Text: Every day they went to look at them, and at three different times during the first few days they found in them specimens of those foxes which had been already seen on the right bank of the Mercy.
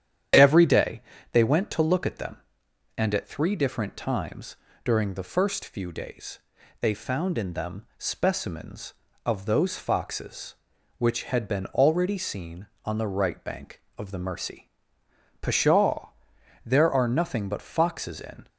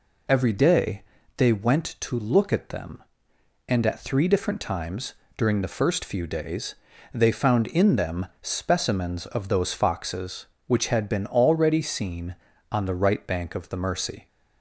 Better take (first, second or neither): second